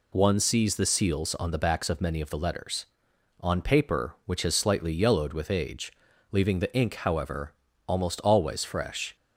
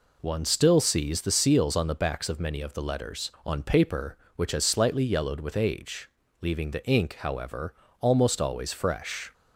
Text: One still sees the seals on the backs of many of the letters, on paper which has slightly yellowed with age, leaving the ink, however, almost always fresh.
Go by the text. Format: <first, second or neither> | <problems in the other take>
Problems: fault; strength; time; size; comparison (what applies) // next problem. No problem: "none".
second | skips "still"; at 0.3 s